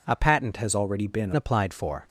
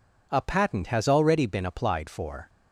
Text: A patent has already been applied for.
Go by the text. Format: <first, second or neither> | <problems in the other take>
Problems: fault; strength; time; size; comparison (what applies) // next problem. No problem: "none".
second | changes voice from "has" to "been"; from 0.5 to 1.3 s; 0.8 s long